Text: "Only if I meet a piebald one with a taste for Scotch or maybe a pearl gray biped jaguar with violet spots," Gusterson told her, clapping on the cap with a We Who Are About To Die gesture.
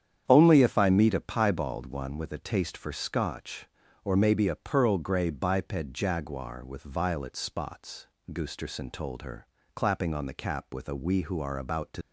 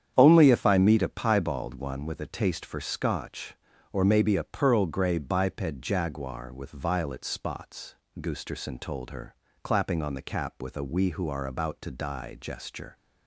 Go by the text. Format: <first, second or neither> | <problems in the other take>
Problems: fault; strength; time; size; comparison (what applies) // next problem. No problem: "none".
second | starts louder than the rest; strong; until 1.2 s; 9 dB; strong in the second // stops before "Die gesture"; at 12.0 s